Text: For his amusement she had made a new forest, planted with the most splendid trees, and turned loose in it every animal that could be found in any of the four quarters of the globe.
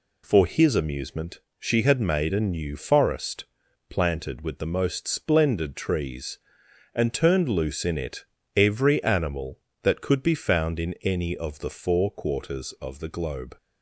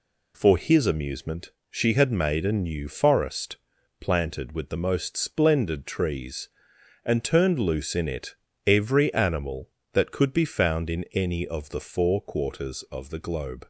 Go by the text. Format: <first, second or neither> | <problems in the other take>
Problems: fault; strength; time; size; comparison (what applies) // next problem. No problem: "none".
neither | pauses between "amusement" and "she"; slight; the same in both // pauses between "it" and "every"; slight; the same in both